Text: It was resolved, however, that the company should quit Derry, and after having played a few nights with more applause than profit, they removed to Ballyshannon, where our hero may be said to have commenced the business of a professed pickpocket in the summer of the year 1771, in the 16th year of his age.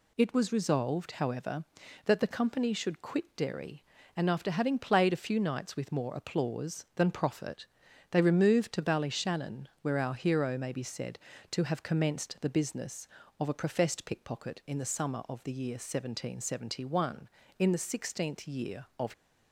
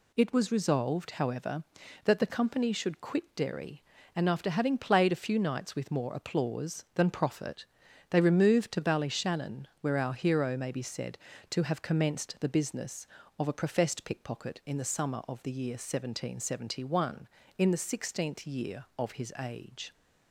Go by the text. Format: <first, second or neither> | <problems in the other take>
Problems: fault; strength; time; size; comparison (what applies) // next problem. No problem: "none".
second | stops before "his age"; at 19.1 s